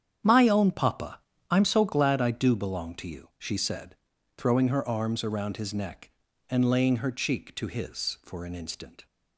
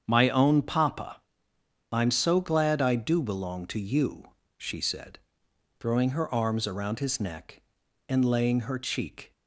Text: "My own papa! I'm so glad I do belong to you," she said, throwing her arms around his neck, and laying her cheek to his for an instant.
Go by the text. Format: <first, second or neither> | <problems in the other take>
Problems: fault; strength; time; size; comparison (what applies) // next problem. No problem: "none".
first | starts louder than the rest; strong; until 1.0 s; 7.5 dB; strong in the first // stops before "to his for an instant"; at 9.3 s